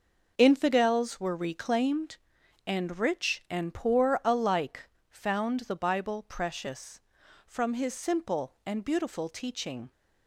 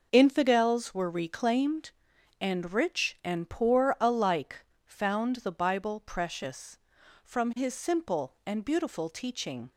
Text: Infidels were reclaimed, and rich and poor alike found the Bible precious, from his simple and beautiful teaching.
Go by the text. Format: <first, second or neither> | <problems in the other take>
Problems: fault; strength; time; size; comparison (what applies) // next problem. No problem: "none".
neither | pauses between "alike" and "found"; slight; the same in both